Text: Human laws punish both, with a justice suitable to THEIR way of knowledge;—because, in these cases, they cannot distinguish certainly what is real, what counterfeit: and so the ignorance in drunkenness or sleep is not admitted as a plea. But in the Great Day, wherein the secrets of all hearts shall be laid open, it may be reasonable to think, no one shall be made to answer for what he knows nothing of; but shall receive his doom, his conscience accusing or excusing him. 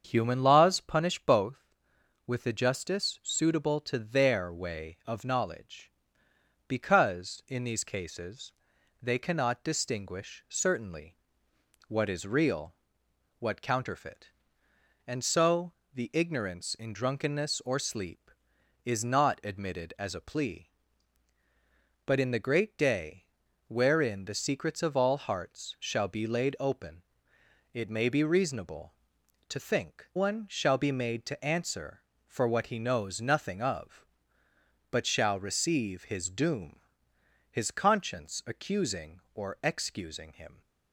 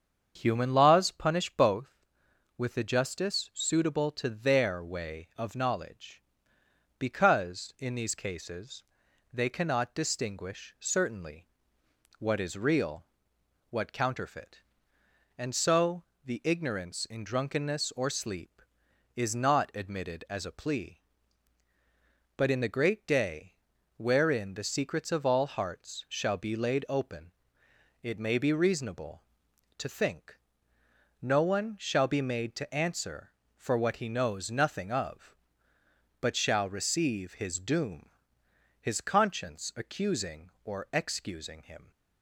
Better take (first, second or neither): second